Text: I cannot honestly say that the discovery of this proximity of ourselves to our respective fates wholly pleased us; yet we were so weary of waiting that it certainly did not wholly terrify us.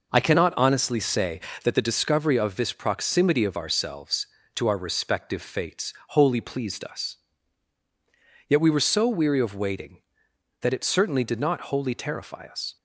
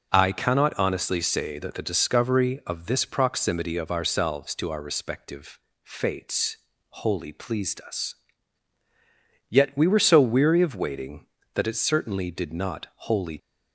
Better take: first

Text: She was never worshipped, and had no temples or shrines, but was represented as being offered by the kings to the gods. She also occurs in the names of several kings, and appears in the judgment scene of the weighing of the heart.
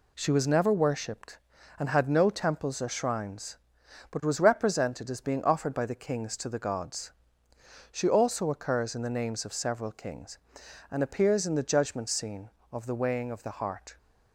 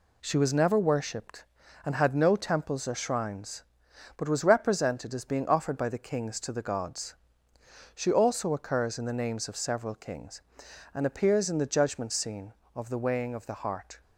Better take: neither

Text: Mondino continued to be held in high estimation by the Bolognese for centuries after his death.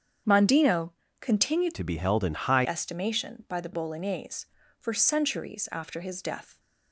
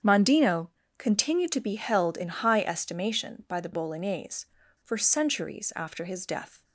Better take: second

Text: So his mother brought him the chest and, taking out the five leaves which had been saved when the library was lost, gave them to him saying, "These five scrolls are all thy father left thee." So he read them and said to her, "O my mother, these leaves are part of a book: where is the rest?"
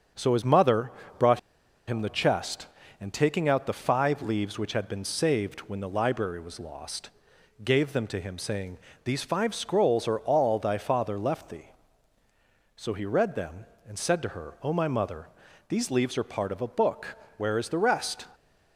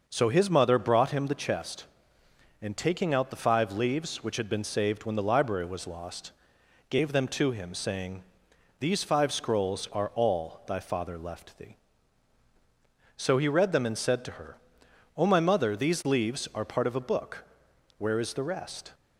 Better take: second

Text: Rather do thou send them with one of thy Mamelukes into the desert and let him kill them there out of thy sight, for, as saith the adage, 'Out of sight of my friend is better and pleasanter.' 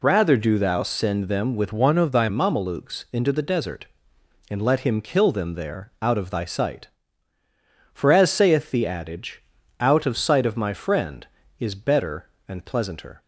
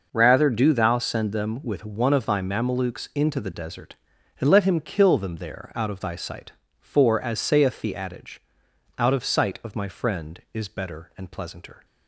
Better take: second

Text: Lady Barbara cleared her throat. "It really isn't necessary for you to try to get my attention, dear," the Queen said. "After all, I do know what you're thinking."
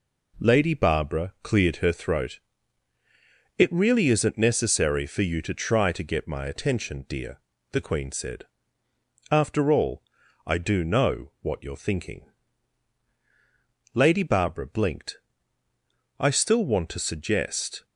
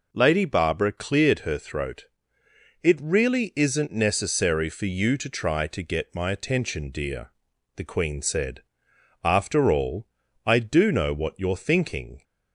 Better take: second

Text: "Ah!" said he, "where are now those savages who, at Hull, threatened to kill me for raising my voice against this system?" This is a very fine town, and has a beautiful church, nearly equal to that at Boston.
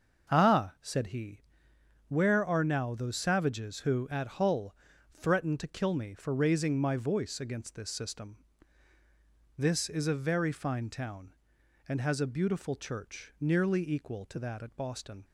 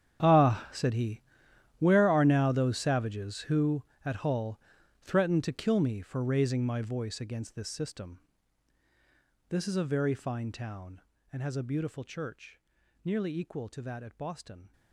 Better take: first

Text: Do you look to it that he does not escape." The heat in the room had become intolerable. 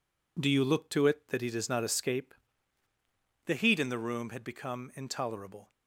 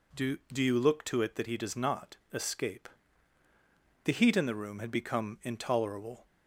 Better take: first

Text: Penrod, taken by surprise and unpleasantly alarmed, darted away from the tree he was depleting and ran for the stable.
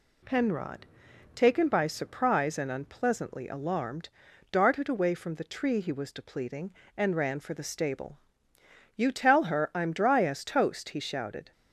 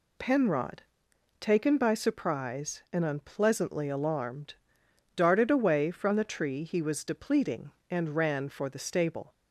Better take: second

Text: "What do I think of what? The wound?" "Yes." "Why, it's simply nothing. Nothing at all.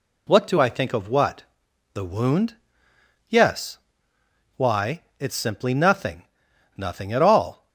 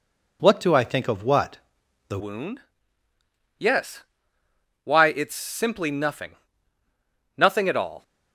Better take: first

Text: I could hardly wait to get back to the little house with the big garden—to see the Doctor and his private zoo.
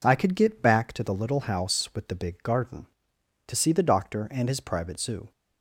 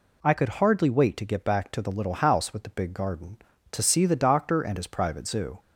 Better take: second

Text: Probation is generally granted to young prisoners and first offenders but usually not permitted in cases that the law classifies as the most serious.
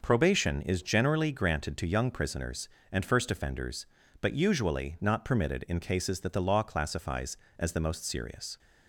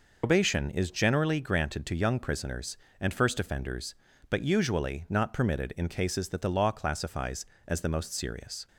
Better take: first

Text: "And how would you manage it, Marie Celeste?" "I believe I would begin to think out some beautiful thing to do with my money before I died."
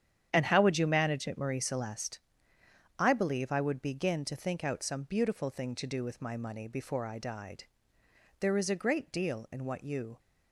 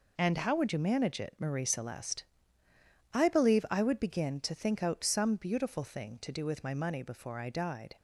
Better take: second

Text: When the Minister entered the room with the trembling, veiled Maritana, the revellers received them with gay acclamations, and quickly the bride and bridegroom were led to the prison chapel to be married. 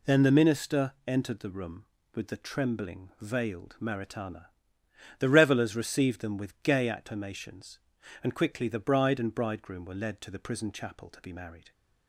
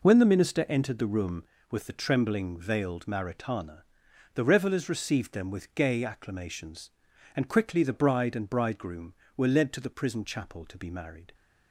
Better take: second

